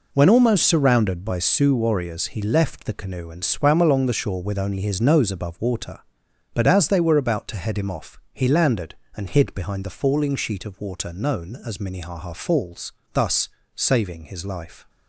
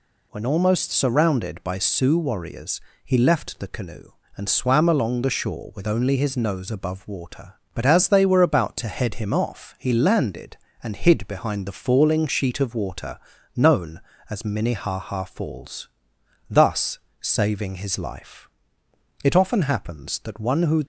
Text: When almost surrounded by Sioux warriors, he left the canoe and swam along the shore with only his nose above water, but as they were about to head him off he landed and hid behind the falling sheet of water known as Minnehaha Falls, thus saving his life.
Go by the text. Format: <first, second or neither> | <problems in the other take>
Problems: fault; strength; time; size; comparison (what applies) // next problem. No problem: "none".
first | pauses between "water" and "known"; slight; at 13.1 s; 0.36 s long // pauses between "thus" and "saving"; slight; at 16.9 s; 0.20 s long; slight in the first // goes on to say "It often happens that one who"; from 19.2 s on; 1.6 s long